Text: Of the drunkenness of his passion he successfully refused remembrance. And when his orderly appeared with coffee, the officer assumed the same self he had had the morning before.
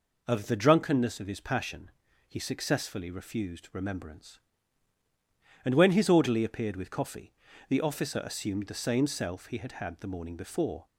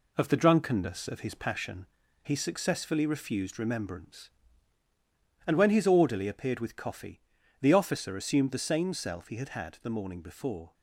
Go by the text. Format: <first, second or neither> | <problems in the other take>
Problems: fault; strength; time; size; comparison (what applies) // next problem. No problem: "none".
first | gets quieter; noticeable; throughout; 4 dB // pauses between "passion" and "he"; slight; at 1.8 s; 0.36 s long; also in the first